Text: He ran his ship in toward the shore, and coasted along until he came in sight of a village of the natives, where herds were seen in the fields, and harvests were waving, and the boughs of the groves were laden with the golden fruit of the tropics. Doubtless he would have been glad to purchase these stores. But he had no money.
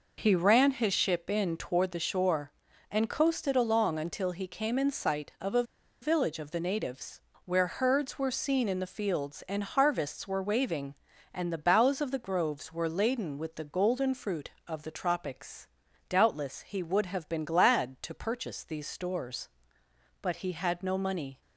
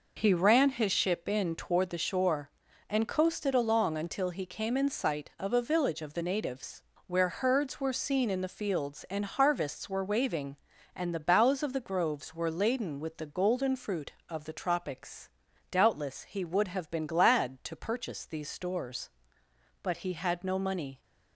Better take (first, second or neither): second